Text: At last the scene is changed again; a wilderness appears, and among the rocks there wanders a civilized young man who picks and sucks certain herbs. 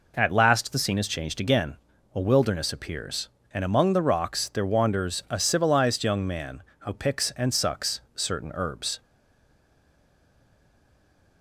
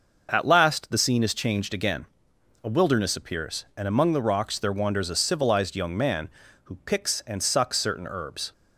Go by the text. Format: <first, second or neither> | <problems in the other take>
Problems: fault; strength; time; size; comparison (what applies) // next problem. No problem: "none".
second | pauses between "sucks" and "certain"; slight; at 7.9 s; 0.16 s long // stays silent after the last word; from 9.0 s on; 2.4 s long